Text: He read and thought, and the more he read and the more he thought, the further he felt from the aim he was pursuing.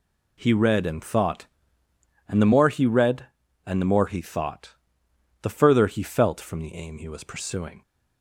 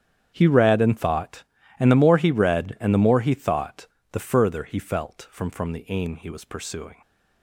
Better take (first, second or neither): first